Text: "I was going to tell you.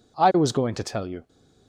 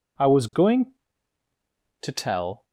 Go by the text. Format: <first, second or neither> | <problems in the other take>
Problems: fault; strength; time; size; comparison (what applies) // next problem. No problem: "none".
first | stops before "you"; at 2.6 s